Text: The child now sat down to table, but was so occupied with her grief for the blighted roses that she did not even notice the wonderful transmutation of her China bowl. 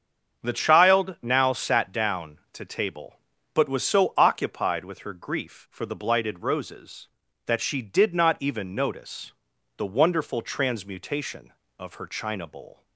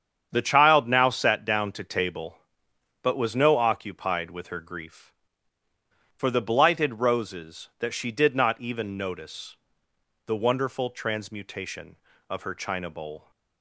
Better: first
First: starts louder than the rest; strong; until 1.4 s; 7.5 dB // pauses between "notice" and "the"; at 9.3 s; 0.42 s long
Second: starts louder than the rest; strong; until 1.3 s; 8 dB // says "no" for "so"; at 3.3 s // pauses between "notice" and "the"; noticeable; at 9.5 s; 0.70 s long

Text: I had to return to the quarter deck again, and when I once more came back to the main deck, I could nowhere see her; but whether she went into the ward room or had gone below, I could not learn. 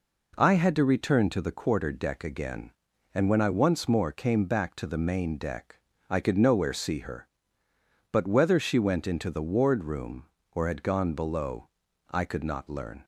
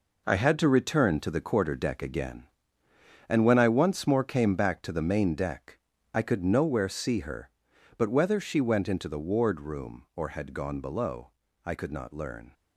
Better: first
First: none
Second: gets quieter; strong; throughout; 8.5 dB

